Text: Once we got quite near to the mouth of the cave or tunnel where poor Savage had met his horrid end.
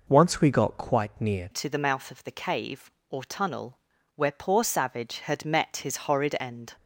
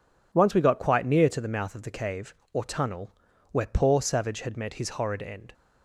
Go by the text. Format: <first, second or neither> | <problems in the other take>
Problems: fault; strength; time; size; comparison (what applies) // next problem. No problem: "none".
second | changes voice at "to"; from 1.5 s on; 5.2 s long // pauses between "tunnel" and "where"; at 3.7 s; 0.38 s long; also in the second